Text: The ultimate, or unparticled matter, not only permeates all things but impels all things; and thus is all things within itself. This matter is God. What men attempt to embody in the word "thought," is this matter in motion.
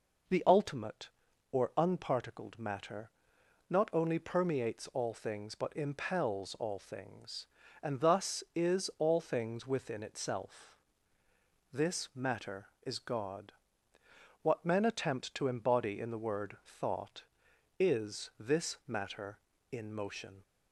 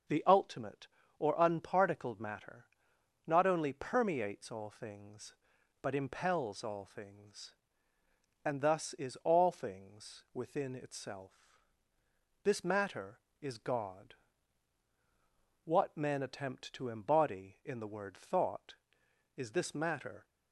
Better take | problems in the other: first | starts louder than the rest; until 1.4 s; 7 dB // stops before "in motion"; at 20.2 s

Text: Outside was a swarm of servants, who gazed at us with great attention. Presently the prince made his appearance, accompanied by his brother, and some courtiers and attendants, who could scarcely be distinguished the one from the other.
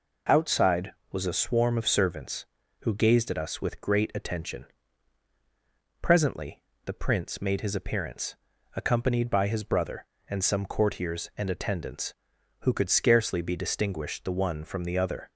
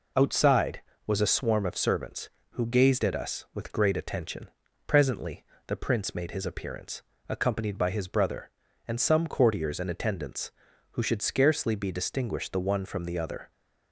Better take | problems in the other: first | pauses between "Presently" and "the"; slight; at 5.4 s; 0.22 s long; slight in the first // says "should" for "could"; at 11.0 s

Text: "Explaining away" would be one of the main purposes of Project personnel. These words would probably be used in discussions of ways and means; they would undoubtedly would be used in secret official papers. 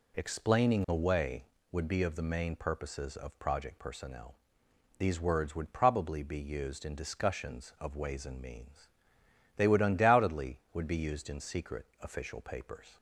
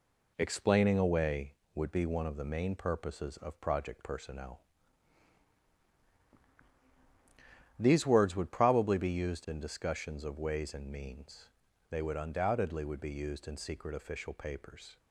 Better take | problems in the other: second | skips "one"; at 2.0 s

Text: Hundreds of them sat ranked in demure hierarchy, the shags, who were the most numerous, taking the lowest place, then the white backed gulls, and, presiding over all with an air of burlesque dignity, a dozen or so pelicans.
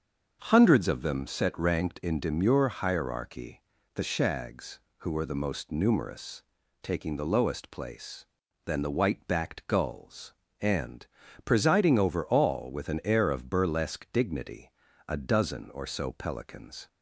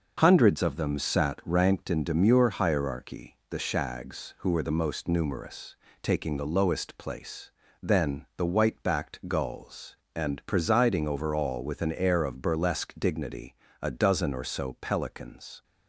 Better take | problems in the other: second | starts louder than the rest; until 1.4 s; 6.5 dB // says "set" for "sat"; at 1.2 s

